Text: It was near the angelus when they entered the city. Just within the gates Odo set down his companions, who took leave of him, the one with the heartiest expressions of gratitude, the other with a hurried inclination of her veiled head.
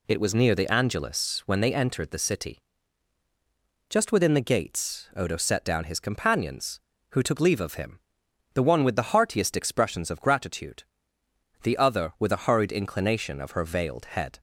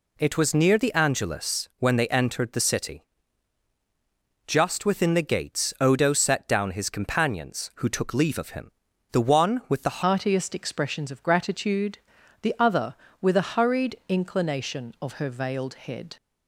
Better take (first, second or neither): first